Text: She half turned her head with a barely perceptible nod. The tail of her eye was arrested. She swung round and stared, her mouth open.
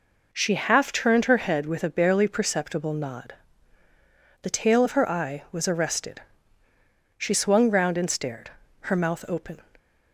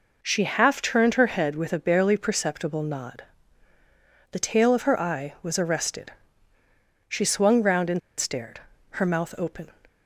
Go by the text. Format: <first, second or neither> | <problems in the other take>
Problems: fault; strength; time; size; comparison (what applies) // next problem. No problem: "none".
first | pauses between "and" and "stared"; slight; at 8.0 s; 0.18 s long